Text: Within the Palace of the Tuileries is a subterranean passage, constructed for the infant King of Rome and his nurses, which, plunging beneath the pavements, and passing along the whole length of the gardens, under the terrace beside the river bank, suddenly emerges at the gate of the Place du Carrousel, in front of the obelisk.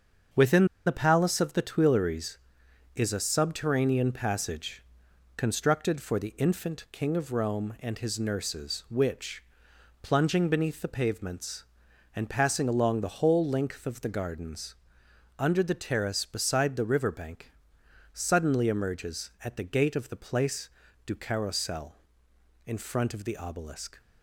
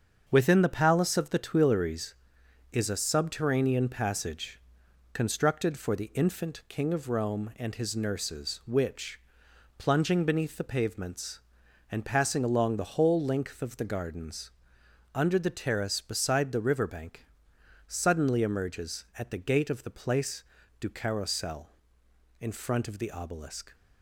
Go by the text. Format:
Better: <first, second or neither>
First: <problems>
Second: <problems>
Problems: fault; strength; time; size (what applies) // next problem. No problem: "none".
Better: second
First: starts louder than the rest; until 1.5 s; 7 dB // pauses between "Within" and "the"; slight; at 0.6 s; 0.20 s long // pauses between "Place" and "du"; at 20.6 s; 0.38 s long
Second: starts louder than the rest; until 1.2 s; 7 dB // pauses between "Place" and "du"; at 20.4 s; 0.38 s long